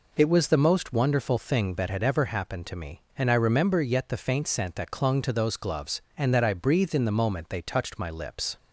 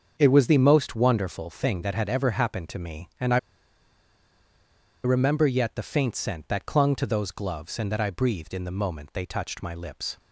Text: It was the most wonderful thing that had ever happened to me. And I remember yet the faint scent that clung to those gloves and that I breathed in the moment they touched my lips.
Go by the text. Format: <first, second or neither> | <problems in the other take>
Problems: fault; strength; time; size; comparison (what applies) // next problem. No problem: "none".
first | starts louder than the rest; until 1.1 s; 7 dB // pauses between "I" and "remember"; strong; at 3.3 s; 1.6 s long